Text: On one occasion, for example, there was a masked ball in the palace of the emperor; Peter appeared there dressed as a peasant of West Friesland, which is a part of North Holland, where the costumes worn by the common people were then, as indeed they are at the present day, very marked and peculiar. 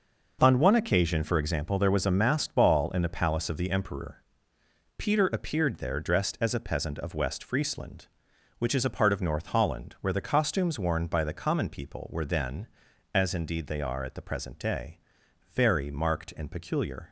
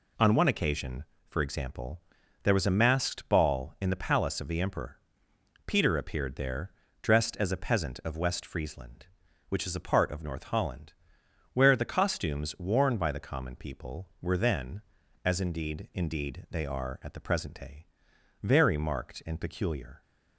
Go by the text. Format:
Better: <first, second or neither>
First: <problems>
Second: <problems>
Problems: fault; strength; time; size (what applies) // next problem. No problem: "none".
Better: first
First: none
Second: pauses between "there" and "dressed"; slight; at 6.7 s; 0.30 s long // says "indeed" twice; at 15.9 s